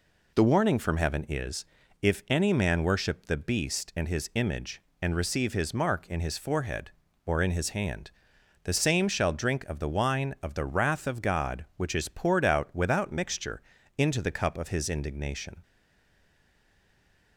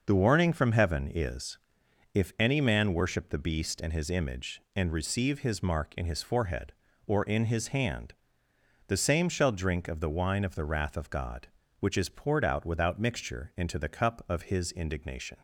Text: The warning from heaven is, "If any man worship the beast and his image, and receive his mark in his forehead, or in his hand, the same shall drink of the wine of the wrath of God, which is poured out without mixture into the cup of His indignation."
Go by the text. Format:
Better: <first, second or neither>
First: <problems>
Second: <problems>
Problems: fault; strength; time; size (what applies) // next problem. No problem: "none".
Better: second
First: pauses between "mixture" and "into"; slight; at 13.6 s; 0.34 s long // stays silent after the last word; noticeable; from 15.6 s on; 1.7 s long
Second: none